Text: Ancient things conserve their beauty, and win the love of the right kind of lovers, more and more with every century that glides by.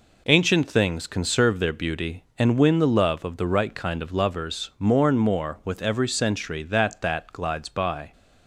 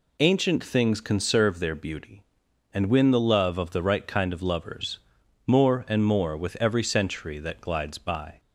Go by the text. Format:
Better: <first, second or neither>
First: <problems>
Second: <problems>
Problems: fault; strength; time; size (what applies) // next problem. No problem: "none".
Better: second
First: says "that" twice; at 7.0 s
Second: none